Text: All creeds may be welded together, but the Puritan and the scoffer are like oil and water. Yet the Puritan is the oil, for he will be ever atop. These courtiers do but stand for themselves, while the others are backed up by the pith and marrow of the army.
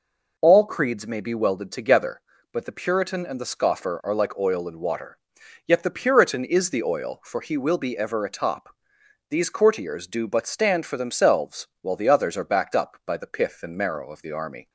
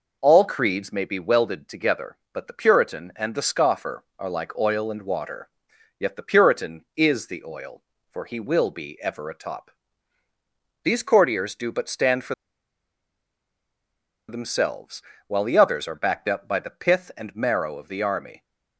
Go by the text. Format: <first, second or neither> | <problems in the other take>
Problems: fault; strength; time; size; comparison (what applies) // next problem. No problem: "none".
first | pauses between "for" and "themselves"; strong; at 12.3 s; 1.9 s long